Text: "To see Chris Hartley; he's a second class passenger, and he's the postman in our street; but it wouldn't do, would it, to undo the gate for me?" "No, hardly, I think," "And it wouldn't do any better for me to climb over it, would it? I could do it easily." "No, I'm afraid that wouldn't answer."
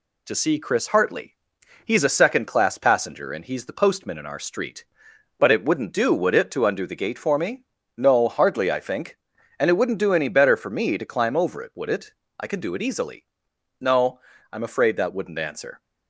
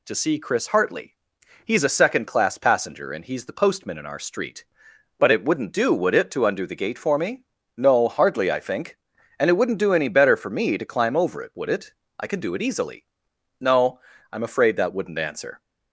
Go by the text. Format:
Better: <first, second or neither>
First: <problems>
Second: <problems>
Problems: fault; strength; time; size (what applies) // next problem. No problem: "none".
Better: second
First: gets quieter; slight; throughout; 2.5 dB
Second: none